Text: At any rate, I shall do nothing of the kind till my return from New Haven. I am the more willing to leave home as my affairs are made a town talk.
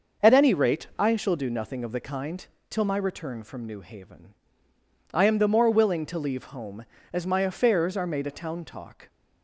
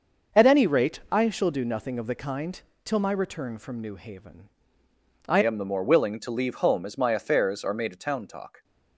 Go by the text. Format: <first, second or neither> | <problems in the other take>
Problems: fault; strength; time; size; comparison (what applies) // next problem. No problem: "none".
first | starts louder than the rest; noticeable; until 1.4 s; 6 dB; noticeable in the first // pauses between "kind" and "till"; slight; at 2.5 s; 0.26 s long; slight in the first // changes voice at "am"; from 5.4 s on; 3.2 s long